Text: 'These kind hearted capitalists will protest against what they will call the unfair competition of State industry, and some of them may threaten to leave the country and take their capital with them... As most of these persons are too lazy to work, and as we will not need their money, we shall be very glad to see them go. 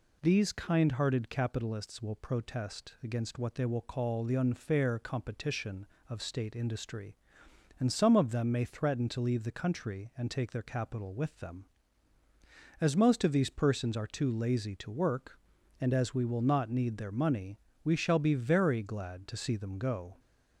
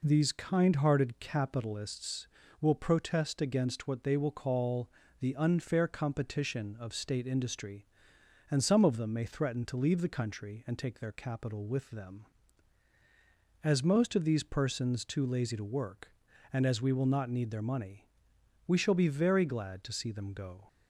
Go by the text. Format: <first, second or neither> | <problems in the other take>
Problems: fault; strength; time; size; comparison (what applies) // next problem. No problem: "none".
first | pauses between "call" and "the"; slight; at 4.8 s; 0.32 s long // skips "are"; at 15.0 s